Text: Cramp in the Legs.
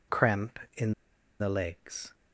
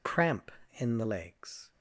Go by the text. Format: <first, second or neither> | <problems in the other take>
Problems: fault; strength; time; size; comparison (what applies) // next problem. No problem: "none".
second | pauses between "in" and "the"; noticeable; at 0.9 s; 0.48 s long